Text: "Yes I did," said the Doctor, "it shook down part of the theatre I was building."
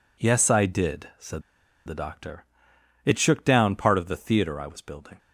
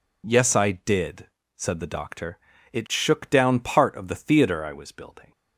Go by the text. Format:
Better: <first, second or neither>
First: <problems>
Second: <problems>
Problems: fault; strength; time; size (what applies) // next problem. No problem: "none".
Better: second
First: pauses between "said" and "the"; at 1.4 s; 0.45 s long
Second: none